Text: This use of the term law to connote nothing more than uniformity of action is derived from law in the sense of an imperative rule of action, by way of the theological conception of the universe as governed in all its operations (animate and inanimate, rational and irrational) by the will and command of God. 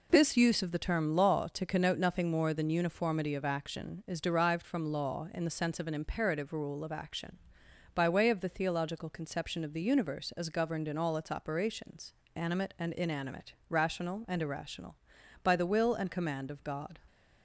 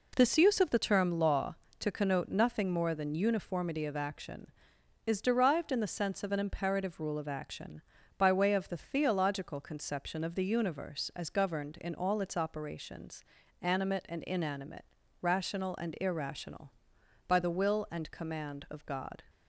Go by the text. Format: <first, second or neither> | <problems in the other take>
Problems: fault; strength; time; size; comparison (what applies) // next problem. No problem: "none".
first | skips "from law"; at 5.7 s